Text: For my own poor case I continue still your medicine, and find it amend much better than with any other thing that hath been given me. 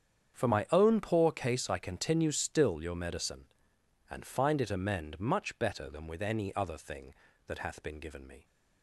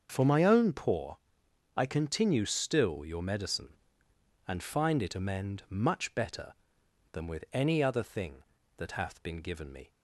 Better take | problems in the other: first | starts louder than the rest; until 1.1 s; 6.5 dB; strong in the first // skips "case"; at 1.4 s

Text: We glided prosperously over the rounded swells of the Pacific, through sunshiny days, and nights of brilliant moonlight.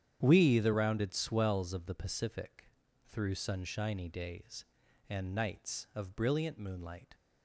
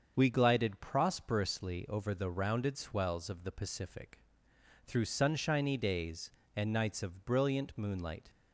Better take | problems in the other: second | starts louder than the rest; strong; until 1.2 s; 9 dB; also in the second // skips "glided prosperously over"; at 0.5 s

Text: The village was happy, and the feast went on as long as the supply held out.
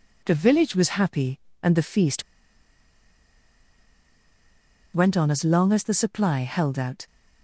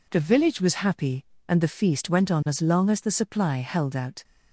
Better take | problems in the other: second | pauses between "feast" and "went"; strong; at 2.2 s; 2.7 s long

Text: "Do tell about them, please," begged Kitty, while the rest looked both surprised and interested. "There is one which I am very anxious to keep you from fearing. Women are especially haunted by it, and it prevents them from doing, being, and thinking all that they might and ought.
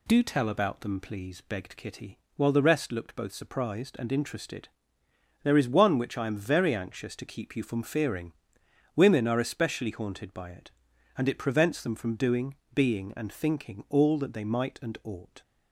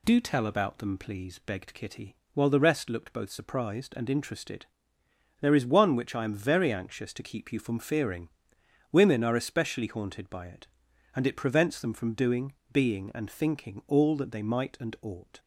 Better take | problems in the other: neither | none

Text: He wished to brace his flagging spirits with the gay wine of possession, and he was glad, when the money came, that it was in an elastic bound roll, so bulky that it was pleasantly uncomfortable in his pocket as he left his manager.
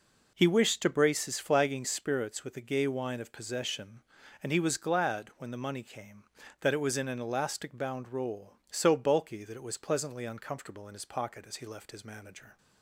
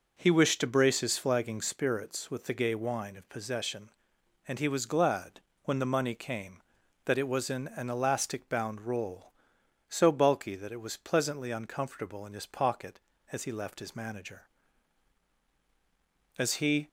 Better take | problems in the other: first | goes on to say "As he"; from 16.3 s on; 0.50 s long

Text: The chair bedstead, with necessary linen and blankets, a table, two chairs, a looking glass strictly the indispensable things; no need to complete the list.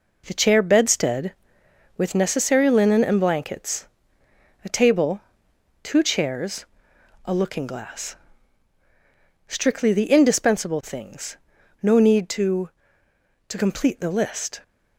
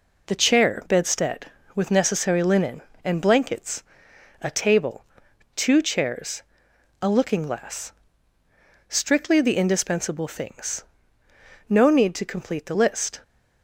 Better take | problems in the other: second | pauses between "glass" and "strictly"; strong; at 8.1 s; 1.3 s long; also in the second // says "to" twice; at 13.4 s

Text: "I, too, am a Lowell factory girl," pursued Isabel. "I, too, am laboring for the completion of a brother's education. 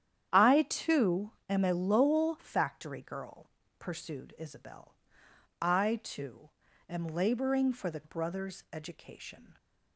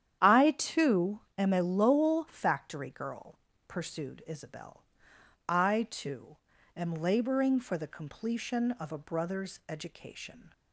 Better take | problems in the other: second | starts louder than the rest; strong; until 1.3 s; 10 dB; strong in the second // skips "completion of a"; at 8.0 s

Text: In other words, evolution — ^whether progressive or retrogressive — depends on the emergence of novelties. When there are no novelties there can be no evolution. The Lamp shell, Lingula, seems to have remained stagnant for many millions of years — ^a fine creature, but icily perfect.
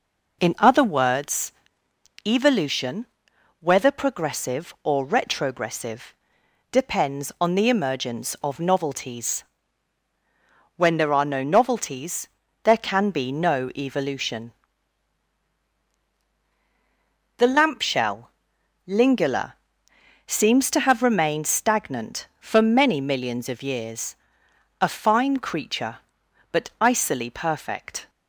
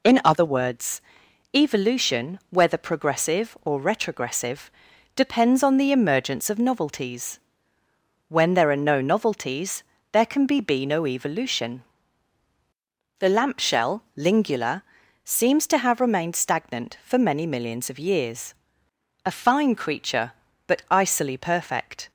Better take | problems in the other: first | pauses between "novelties" and "there"; slight; at 9.8 s; 0.30 s long; slight in the first // says "be" twice; at 10.6 s

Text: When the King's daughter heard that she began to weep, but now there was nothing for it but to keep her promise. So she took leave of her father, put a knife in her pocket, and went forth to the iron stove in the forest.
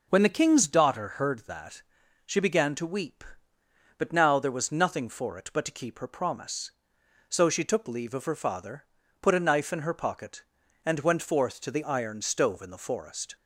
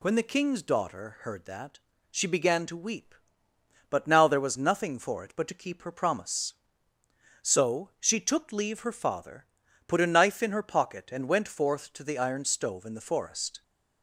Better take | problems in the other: first | pauses between "that" and "she"; slight; at 1.7 s; 0.32 s long; also in the first // skips "of"; at 8.8 s

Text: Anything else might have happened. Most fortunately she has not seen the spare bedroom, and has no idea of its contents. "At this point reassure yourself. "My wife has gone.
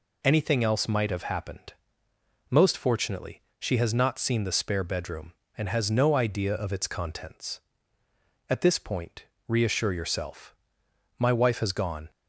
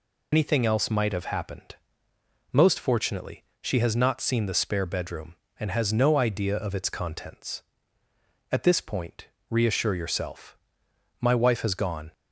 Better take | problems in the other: first | loses the start of "Anything"; at 0.3 s; 65 ms // pauses between "fortunately" and "she"; slight; at 3.4 s; 0.18 s long; slight in the first // pauses between "point" and "reassure"; slight; at 9.2 s; 0.24 s long; slight in the first

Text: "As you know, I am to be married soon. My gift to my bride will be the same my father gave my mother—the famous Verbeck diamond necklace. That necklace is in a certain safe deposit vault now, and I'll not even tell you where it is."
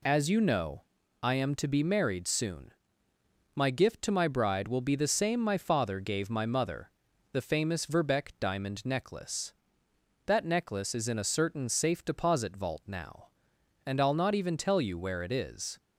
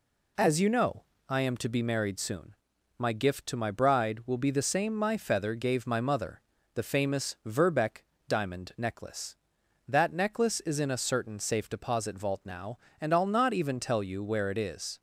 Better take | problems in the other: first | says "feather" for "father"; at 5.1 s // pauses between "Verbeck" and "diamond"; slight; at 8.0 s; 0.26 s long

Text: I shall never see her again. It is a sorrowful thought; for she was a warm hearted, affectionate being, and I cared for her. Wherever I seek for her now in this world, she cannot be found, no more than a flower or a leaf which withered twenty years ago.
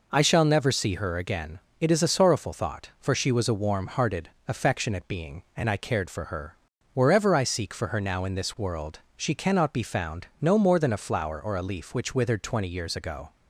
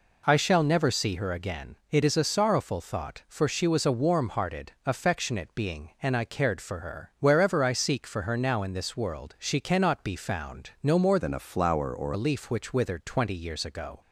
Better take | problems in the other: first | changes voice from "than" to "or"; from 11.1 to 12.1 s; 1.0 s long

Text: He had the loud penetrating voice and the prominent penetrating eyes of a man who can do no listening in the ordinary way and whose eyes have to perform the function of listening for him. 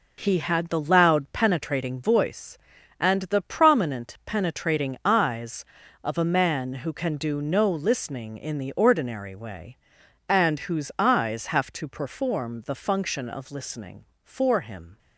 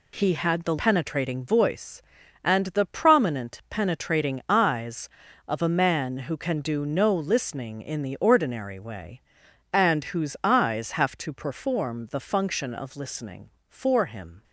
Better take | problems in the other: first | skips "loud"; at 0.7 s

